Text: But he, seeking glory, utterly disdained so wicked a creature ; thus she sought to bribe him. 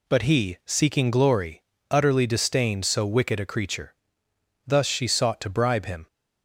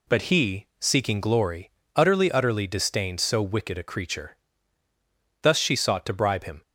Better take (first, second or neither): first